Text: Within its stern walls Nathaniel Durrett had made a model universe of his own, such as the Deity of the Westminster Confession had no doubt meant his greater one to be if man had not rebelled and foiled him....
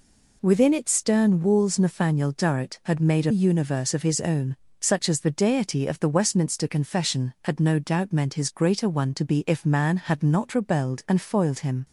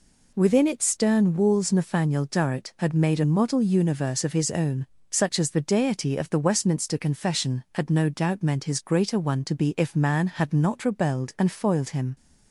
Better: second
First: skips "model"; at 3.3 s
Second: none

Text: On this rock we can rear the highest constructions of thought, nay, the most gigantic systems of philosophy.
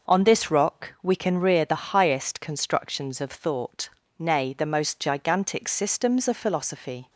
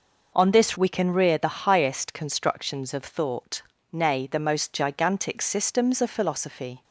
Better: first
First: none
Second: skips "rock"; at 0.7 s

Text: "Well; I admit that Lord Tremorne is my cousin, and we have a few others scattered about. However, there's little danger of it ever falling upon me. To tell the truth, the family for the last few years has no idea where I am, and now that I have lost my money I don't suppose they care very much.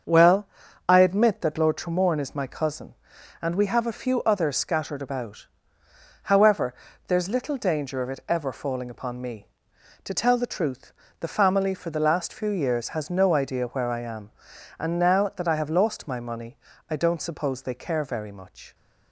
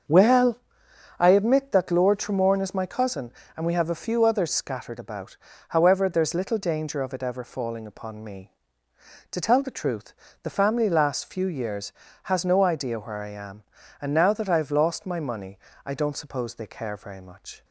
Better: first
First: starts louder than the rest; until 1.4 s; 7 dB // pauses between "money" and "I"; slight; at 16.5 s; 0.32 s long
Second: starts louder than the rest; until 1.6 s; 7 dB // skips "for the"; at 10.9 s // pauses between "money" and "I"; slight; at 15.5 s; 0.28 s long

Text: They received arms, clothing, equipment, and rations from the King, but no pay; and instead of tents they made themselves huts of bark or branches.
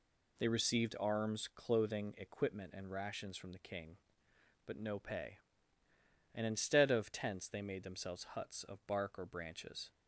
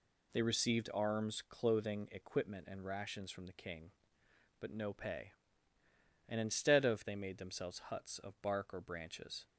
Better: first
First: none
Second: skips "tents"; at 7.0 s

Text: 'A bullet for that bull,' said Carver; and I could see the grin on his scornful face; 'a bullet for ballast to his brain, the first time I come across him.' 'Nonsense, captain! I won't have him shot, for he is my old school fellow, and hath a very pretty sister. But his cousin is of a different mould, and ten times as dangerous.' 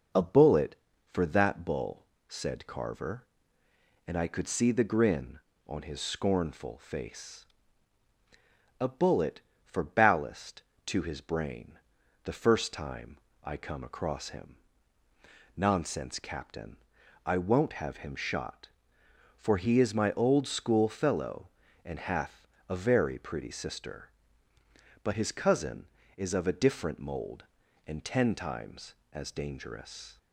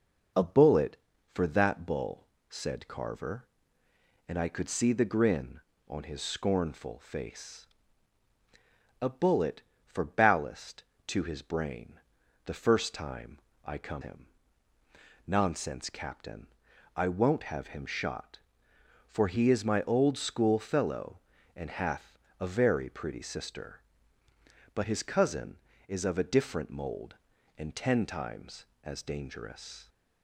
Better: first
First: pauses between "time" and "I"; slight; at 13.1 s; 0.26 s long // pauses between "hath" and "a"; slight; at 22.4 s; 0.22 s long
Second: pauses between "time" and "I"; slight; at 13.3 s; 0.26 s long // skips "across"; at 14.0 s // pauses between "hath" and "a"; slight; at 22.1 s; 0.22 s long

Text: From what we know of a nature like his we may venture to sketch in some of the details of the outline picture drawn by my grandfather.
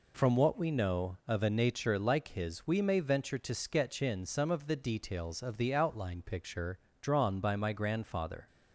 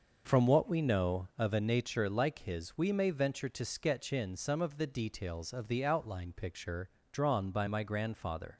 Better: first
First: pauses between "picture" and "drawn"; slight; at 6.7 s; 0.24 s long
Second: starts louder than the rest; noticeable; until 1.5 s; 6 dB // pauses between "picture" and "drawn"; slight; at 6.8 s; 0.24 s long

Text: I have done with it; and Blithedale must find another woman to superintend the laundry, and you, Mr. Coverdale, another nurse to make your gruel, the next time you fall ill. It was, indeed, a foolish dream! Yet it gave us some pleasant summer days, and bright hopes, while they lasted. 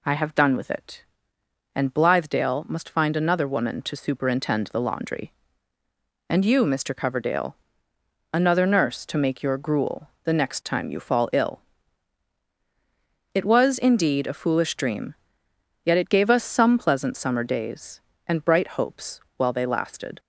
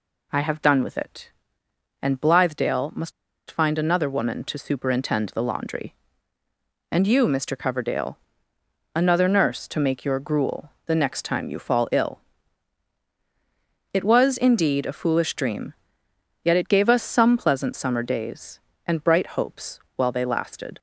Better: first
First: none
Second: pauses between "must" and "find"; at 3.1 s; 0.38 s long

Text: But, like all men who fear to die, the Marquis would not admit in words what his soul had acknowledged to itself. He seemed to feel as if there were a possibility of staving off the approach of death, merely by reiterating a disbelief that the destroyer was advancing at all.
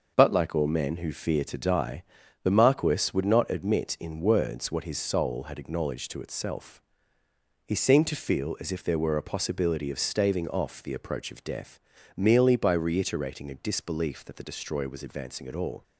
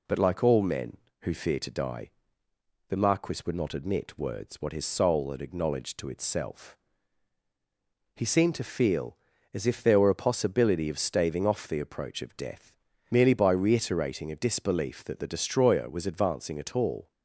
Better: first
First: none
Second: skips "in"; at 4.1 s

